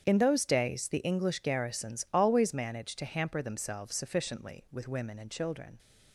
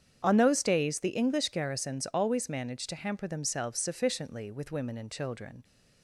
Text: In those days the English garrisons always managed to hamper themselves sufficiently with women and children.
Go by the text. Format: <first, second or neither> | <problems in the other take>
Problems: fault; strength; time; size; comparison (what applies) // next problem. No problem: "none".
first | starts louder than the rest; strong; until 1.2 s; 8 dB; strong in the first // says "On" for "In"; at 0.2 s